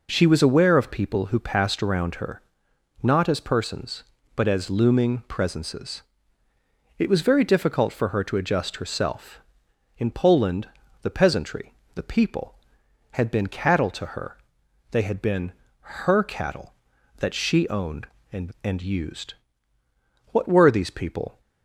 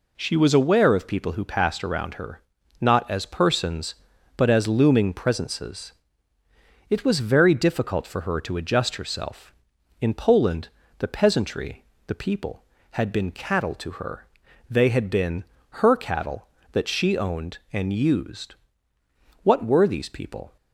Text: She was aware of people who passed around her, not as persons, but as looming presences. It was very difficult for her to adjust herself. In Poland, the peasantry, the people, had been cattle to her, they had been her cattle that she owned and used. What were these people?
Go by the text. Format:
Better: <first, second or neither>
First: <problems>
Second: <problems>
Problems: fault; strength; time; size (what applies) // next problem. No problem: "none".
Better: second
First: pauses between "been" and "her"; slight; at 15.5 s; 0.30 s long // says "and" twice; at 18.6 s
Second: pauses between "been" and "her"; slight; at 15.4 s; 0.26 s long